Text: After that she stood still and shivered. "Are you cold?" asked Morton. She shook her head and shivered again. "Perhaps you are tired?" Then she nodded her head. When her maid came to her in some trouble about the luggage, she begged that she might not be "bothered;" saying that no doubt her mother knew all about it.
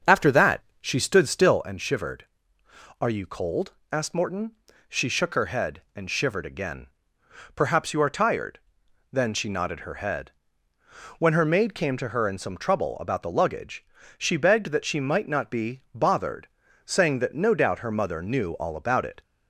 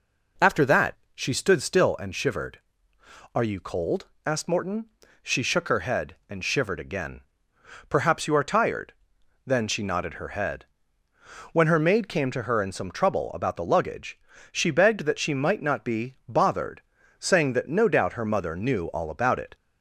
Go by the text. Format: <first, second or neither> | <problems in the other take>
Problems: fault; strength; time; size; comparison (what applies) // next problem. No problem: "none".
second | starts louder than the rest; until 1.6 s; 7 dB // pauses between "that" and "she"; slight; at 0.6 s; 0.20 s long; slight in the second